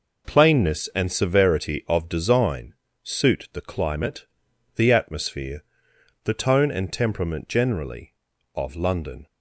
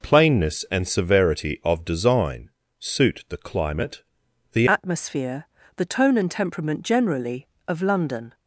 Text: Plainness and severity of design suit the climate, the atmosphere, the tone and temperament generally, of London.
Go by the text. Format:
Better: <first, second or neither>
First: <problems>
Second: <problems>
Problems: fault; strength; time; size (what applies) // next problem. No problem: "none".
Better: first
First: pauses between "design" and "suit"; slight; at 2.7 s; 0.30 s long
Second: pauses between "design" and "suit"; slight; at 2.4 s; 0.30 s long // changes voice at "atmosphere"; from 4.6 s on; 3.7 s long